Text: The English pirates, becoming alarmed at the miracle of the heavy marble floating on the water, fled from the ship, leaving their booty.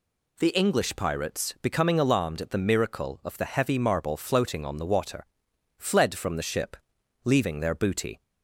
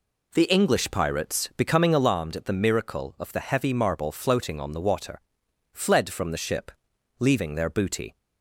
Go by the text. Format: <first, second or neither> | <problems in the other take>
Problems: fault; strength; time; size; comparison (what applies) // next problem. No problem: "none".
first | starts louder than the rest; slight; until 2.1 s; 3 dB